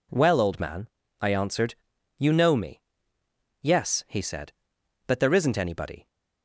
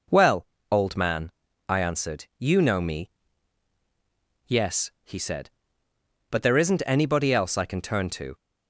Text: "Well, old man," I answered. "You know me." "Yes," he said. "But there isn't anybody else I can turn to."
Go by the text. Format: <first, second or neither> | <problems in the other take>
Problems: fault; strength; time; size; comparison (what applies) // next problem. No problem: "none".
second | stops before "else I can turn to"; at 6.0 s